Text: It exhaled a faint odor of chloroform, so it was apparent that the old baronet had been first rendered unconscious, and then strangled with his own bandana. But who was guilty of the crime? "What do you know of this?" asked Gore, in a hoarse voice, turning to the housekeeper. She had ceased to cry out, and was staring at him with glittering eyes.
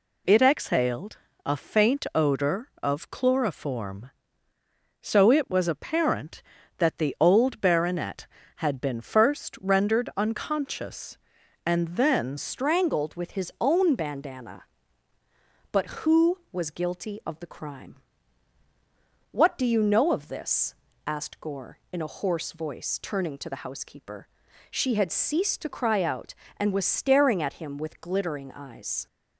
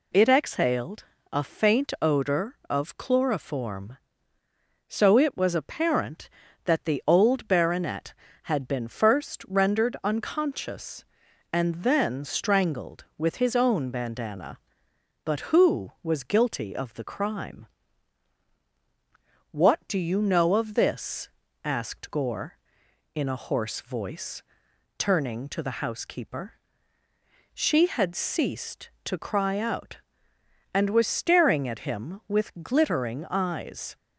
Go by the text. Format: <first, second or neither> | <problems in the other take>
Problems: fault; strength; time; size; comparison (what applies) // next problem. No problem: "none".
second | pauses between "exhaled" and "a"; slight; at 1.1 s; 0.26 s long; slight in the second // changes voice at "strangled"; from 12.3 s on; 16.7 s long